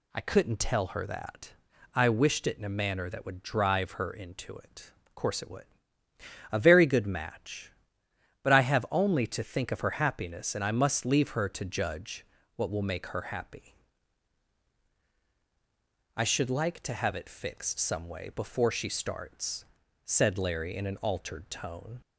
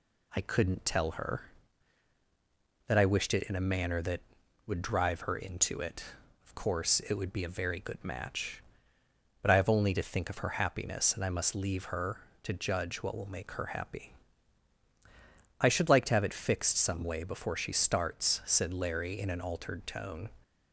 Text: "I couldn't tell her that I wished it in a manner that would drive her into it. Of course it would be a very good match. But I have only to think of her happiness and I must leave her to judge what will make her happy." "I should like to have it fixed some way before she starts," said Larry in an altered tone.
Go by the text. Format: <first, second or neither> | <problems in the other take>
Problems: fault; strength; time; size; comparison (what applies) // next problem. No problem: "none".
second | pauses between "that" and "I"; at 1.5 s; 0.42 s long // skips "be"; at 6.0 s // pauses between "judge" and "what"; slight; at 12.2 s; 0.30 s long